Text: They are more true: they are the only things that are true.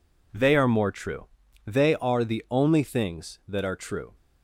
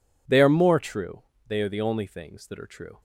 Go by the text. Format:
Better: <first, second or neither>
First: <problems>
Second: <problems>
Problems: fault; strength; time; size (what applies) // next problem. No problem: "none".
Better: neither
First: none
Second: none